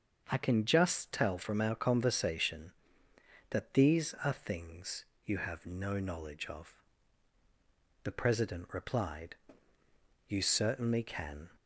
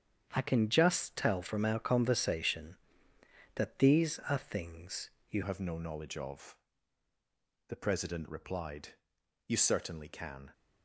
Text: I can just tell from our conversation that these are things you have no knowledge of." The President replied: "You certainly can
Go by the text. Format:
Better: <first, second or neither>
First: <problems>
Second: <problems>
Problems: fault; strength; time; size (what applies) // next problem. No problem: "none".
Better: first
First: starts louder than the rest; until 1.3 s; 6.5 dB // pauses between "things" and "you"; slight; at 5.0 s; 0.22 s long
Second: starts louder than the rest; strong; until 1.3 s; 8 dB // pauses between "things" and "you"; slight; at 5.0 s; 0.22 s long // changes voice at "have"; from 5.4 s on; 5.1 s long